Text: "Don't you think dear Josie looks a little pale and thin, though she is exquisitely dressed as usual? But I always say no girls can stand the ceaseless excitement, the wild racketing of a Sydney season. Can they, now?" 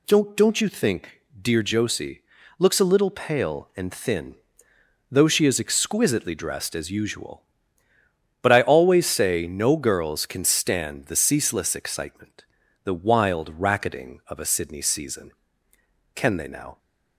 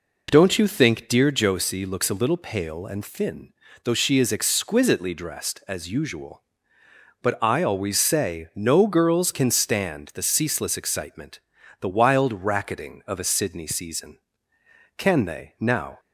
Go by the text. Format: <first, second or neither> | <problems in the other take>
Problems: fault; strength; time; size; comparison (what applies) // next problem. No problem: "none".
second | says "Don't" twice; at 0.3 s // pauses between "think" and "dear"; slight; at 1.2 s; 0.20 s long // pauses between "Josie" and "looks"; slight; at 2.2 s; 0.34 s long